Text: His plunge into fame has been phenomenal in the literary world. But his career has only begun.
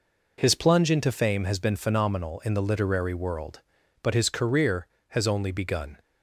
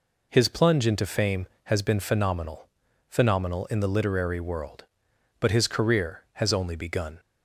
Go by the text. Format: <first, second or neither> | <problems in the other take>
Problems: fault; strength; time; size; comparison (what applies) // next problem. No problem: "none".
first | says "phenomenal" twice; at 3.0 s